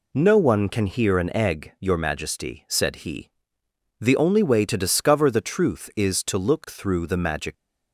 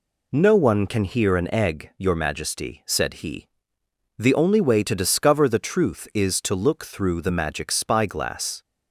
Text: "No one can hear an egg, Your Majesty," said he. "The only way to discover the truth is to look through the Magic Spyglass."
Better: second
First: stops before "Spyglass"; at 7.5 s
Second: none

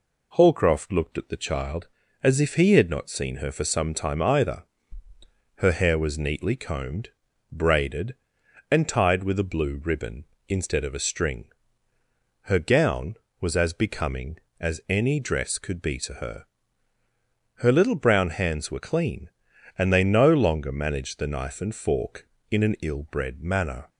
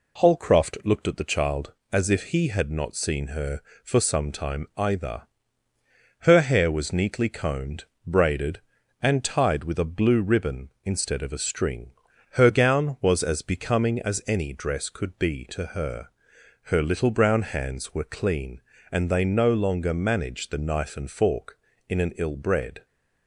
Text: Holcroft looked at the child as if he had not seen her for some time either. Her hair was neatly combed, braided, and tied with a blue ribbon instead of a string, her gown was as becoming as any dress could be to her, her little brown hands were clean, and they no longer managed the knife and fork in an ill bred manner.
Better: first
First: none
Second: stops before "manner"; at 22.8 s

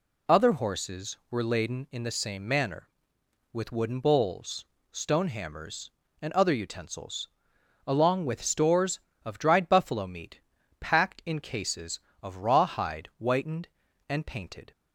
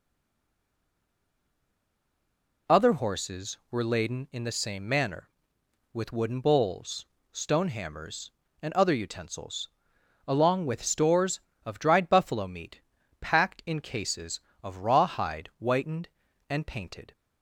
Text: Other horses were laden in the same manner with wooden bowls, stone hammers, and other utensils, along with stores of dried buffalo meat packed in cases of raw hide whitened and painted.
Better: first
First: pauses between "meat" and "packed"; at 10.3 s; 0.40 s long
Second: stays silent before the first word; strong; until 2.6 s; 2.6 s long // pauses between "meat" and "packed"; at 12.7 s; 0.40 s long

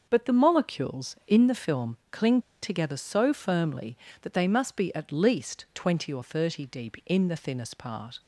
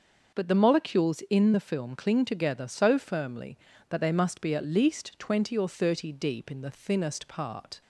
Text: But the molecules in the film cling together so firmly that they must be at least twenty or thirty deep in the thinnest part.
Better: second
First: starts louder than the rest; until 1.1 s; 6.5 dB // pauses between "cling" and "together"; slight; at 2.3 s; 0.22 s long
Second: starts louder than the rest; until 1.4 s; 6.5 dB

